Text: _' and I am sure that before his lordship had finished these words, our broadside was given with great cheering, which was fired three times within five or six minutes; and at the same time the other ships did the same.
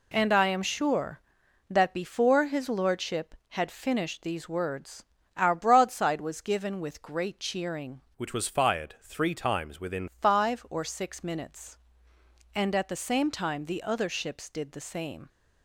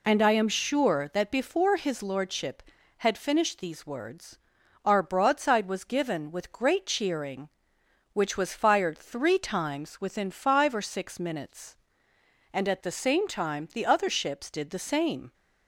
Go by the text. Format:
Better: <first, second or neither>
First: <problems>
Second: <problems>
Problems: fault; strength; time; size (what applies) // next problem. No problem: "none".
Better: second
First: changes voice from "which" to "within"; from 8.1 to 10.0 s; 1.9 s long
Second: none